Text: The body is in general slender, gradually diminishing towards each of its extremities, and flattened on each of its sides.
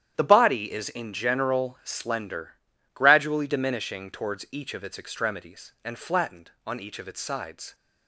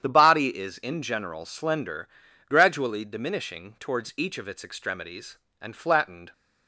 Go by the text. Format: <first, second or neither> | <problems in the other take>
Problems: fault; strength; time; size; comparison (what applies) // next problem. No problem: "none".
first | starts louder than the rest; strong; until 1.0 s; 9.5 dB; strong in the first // stops before "on each of its sides"; at 6.3 s